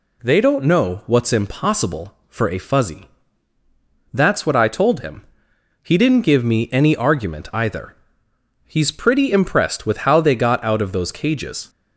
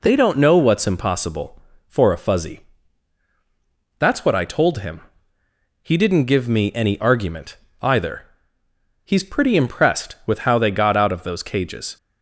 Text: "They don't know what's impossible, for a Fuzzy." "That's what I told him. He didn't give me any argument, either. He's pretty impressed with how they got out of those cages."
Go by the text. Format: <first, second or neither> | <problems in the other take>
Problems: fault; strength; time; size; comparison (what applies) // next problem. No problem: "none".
neither | none